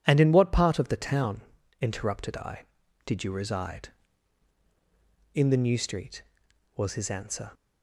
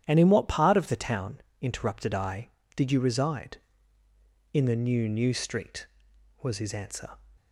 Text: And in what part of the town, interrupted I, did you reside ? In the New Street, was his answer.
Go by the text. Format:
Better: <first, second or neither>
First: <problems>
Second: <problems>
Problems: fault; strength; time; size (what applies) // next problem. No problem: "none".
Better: first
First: none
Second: starts louder than the rest; strong; until 1.0 s; 10 dB // says "New" twice; at 5.0 s